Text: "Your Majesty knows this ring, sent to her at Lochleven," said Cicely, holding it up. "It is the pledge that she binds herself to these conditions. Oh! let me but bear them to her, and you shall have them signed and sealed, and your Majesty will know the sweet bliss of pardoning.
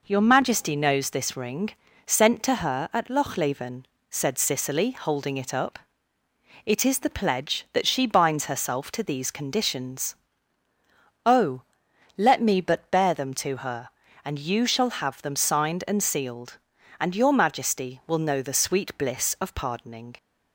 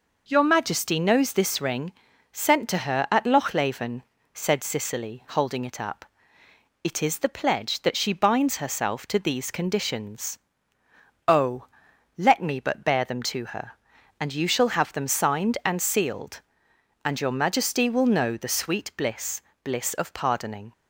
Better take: first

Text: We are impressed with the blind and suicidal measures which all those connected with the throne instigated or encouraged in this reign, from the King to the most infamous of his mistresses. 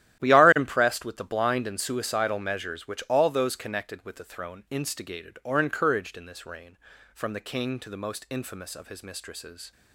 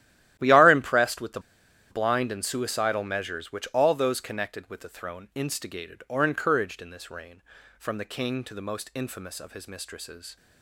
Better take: first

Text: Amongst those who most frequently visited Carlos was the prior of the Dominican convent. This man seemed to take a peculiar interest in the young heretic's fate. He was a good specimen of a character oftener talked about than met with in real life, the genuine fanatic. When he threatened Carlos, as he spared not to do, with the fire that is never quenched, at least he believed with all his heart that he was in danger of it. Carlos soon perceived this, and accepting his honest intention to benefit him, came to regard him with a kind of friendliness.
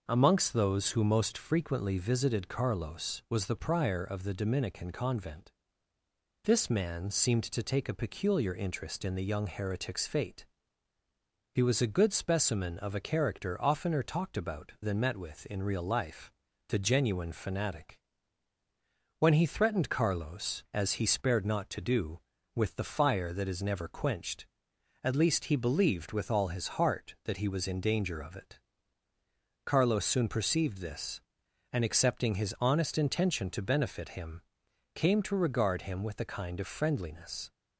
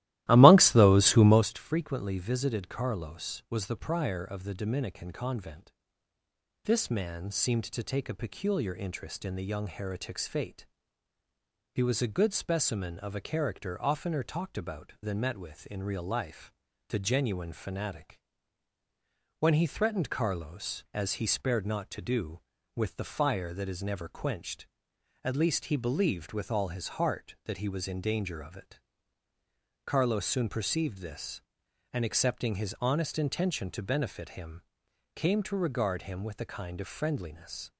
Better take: first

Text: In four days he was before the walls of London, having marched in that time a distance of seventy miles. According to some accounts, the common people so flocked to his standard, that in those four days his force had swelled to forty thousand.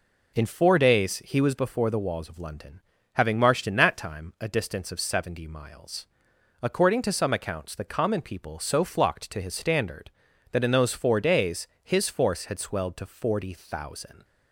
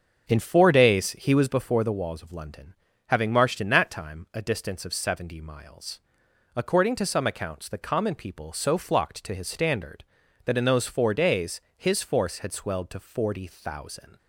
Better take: first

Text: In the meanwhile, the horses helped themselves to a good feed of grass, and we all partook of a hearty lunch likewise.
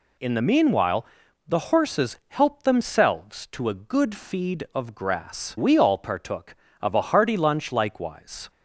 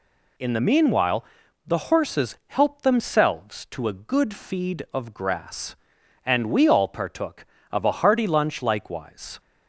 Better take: second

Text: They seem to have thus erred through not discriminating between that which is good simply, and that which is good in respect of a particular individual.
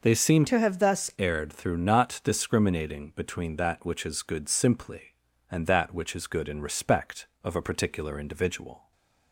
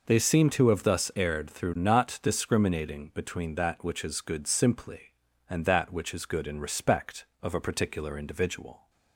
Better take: second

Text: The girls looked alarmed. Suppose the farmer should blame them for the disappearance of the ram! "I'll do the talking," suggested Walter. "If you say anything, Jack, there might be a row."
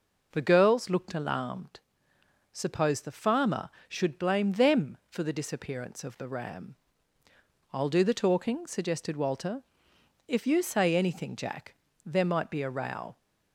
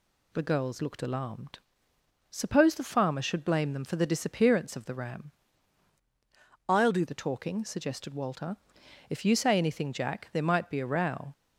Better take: first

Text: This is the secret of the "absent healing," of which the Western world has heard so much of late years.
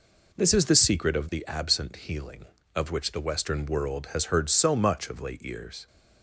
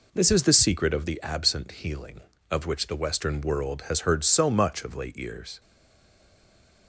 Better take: first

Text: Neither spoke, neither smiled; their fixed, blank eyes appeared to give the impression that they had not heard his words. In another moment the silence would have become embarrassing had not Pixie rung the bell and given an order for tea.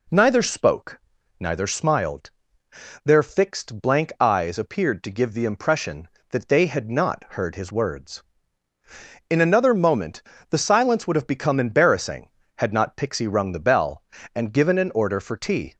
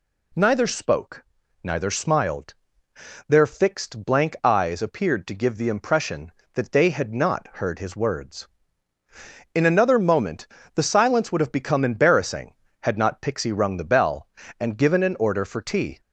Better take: second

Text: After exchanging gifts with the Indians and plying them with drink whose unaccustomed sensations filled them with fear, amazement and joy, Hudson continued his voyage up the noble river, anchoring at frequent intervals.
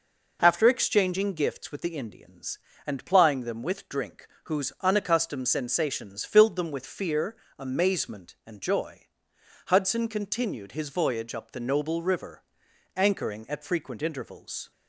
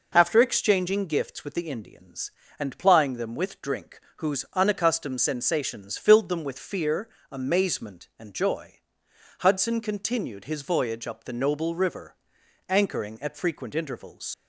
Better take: first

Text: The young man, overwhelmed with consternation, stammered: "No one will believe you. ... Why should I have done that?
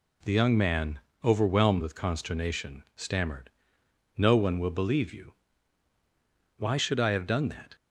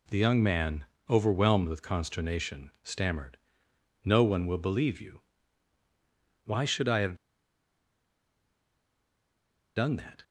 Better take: first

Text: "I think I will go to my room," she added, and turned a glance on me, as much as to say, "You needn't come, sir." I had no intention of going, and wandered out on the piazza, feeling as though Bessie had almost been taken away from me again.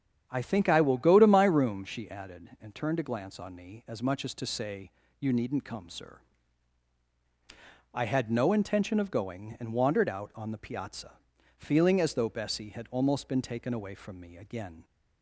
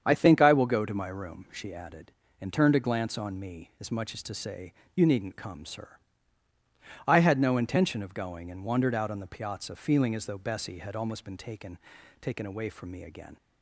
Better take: first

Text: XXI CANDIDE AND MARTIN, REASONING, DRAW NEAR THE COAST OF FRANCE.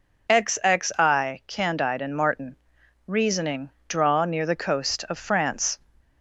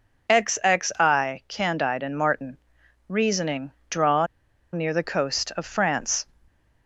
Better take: first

